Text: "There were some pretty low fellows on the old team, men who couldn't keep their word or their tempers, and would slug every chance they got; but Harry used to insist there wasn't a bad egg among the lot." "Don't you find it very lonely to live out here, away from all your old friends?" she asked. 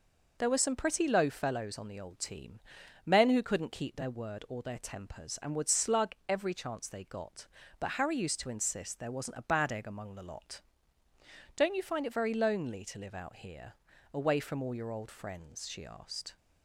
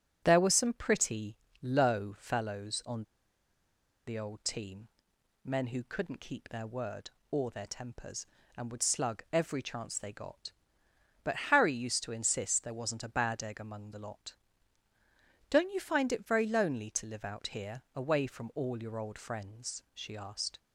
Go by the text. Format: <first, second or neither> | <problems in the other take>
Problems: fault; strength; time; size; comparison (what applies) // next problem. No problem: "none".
first | starts louder than the rest; strong; until 1.2 s; 9.5 dB // pauses between "pretty" and "low"; slight; at 1.3 s; 0.24 s long // pauses between "on" and "the"; at 3.0 s; 1.0 s long